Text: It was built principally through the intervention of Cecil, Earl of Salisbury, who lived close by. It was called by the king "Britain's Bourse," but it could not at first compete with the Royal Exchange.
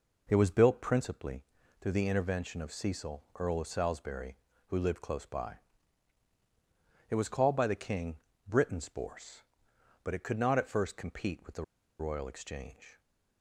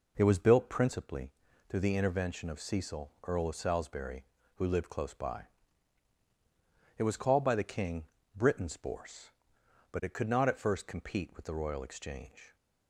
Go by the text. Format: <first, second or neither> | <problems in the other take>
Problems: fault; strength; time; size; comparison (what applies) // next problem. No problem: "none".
second | pauses between "principally" and "through"; slight; at 1.4 s; 0.36 s long; slight in the second // pauses between "king" and "Britain's"; slight; at 8.1 s; 0.30 s long; slight in the second // pauses between "the" and "Royal"; slight; at 11.6 s; 0.35 s long